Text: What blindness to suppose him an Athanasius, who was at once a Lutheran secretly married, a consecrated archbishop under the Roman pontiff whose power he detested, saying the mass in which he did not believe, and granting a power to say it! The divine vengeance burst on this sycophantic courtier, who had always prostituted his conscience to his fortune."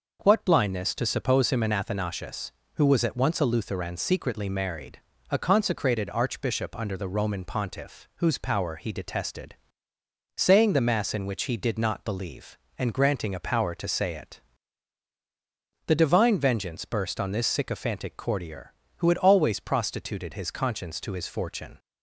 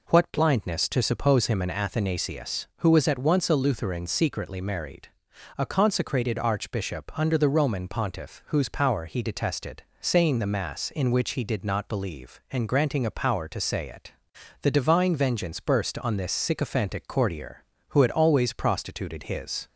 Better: first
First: none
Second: stops before "conscience to his fortune"; at 19.6 s

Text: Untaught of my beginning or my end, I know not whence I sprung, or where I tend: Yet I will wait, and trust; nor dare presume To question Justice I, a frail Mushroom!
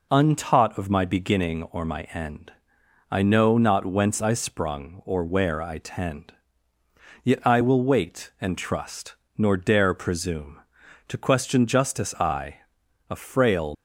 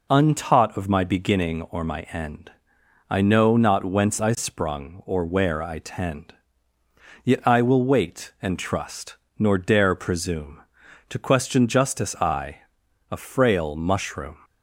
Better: second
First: stops before "Mushroom"; at 13.7 s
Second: none

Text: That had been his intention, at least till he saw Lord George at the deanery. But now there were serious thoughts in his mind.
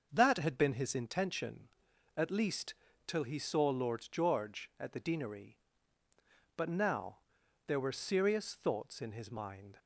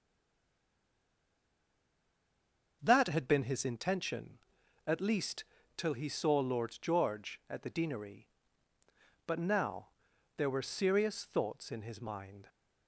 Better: first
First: starts louder than the rest; until 1.1 s; 6.5 dB // pauses between "least" and "till"; slight; at 2.7 s; 0.32 s long // pauses between "now" and "there"; noticeable; at 7.1 s; 0.48 s long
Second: stays silent before the first word; strong; until 2.8 s; 2.8 s long // starts louder than the rest; until 3.8 s; 6.5 dB // pauses between "least" and "till"; slight; at 5.4 s; 0.32 s long // pauses between "now" and "there"; noticeable; at 9.8 s; 0.48 s long

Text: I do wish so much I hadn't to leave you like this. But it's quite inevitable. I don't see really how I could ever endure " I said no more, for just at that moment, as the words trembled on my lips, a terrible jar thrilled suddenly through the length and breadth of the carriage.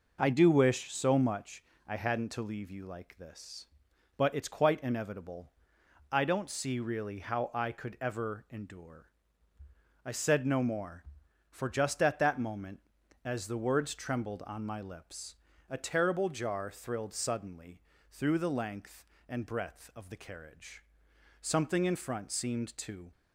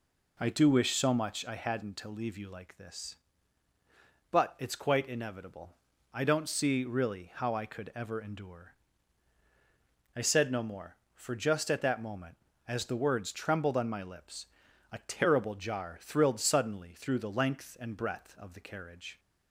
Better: second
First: starts louder than the rest; noticeable; until 1.2 s; 6 dB // pauses between "much" and "I"; slight; at 1.6 s; 0.24 s long // pauses between "suddenly" and "through"; slight; at 17.8 s; 0.30 s long // goes on to say "Something in front seemed to"; strong; from 21.4 s on; 1.7 s long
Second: none

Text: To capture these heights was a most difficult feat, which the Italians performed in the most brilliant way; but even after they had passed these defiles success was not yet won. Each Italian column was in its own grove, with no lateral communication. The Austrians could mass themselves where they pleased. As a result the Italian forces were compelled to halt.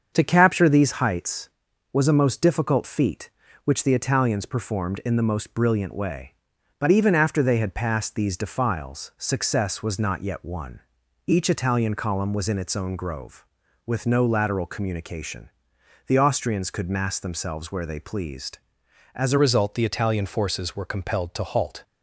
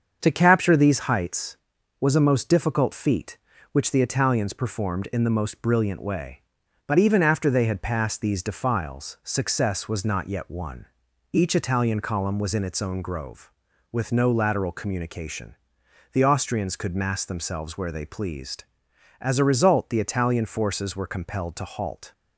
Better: second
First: starts louder than the rest; until 1.1 s; 7 dB // changes voice at "result"; from 19.3 s on; 2.5 s long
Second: starts louder than the rest; until 1.2 s; 7 dB

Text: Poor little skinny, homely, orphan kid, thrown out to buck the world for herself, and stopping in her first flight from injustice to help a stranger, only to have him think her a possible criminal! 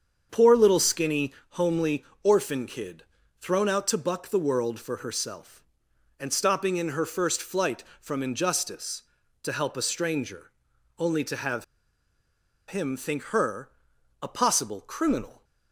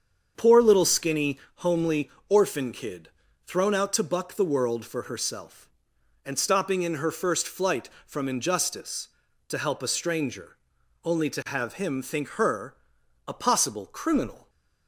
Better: second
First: starts louder than the rest; strong; until 1.3 s; 7 dB // pauses between "have" and "him"; at 11.6 s; 1.0 s long // pauses between "her" and "a"; noticeable; at 13.6 s; 0.52 s long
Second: starts louder than the rest; strong; until 1.3 s; 7 dB // pauses between "her" and "a"; noticeable; at 12.7 s; 0.52 s long

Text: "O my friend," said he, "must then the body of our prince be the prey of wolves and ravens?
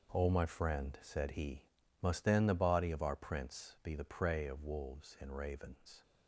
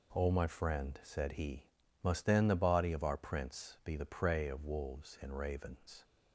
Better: second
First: gets quieter; strong; throughout; 12 dB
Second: none

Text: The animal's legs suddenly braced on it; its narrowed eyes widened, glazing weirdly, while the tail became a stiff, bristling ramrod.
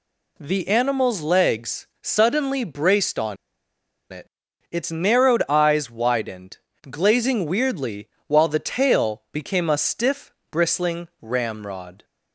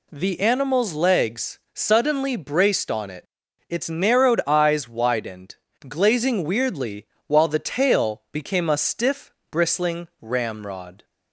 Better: second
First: pauses between "legs" and "suddenly"; slight; at 1.8 s; 0.16 s long // pauses between "on" and "it"; noticeable; at 3.3 s; 0.76 s long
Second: pauses between "legs" and "suddenly"; slight; at 1.5 s; 0.16 s long

